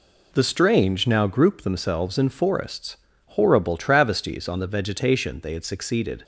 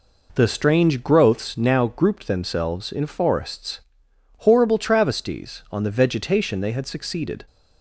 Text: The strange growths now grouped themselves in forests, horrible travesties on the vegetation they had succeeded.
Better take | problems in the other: second | skips "growths"; at 1.0 s

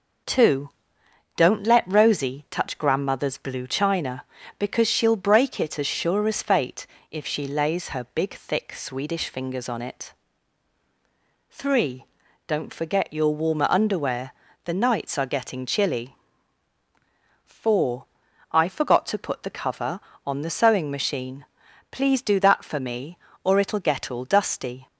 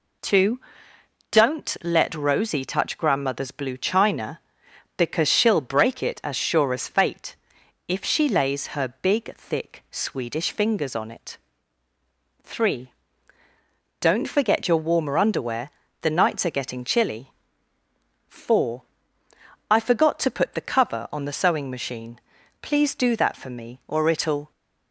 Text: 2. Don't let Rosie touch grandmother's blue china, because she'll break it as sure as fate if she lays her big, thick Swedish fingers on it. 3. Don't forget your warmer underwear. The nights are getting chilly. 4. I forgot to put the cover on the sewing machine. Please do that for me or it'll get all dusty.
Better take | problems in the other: first | pauses between "fate" and "if"; noticeable; at 7.3 s; 0.52 s long; slight in the first // stops before "get all dusty"; at 24.5 s

